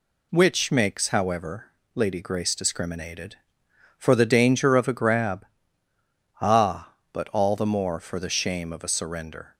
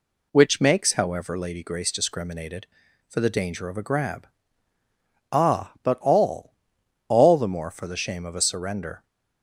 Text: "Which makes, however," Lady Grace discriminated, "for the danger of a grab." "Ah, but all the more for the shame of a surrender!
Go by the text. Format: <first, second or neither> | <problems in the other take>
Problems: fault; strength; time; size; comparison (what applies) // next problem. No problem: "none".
first | says "all" twice; at 7.0 s